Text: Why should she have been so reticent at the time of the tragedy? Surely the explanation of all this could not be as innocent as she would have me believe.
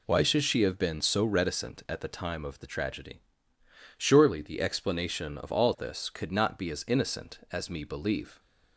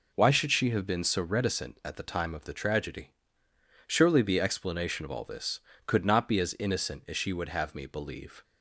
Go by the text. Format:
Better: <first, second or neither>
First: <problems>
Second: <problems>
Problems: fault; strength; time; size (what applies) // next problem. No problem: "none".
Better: second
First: skips "she would have"; at 7.6 s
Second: none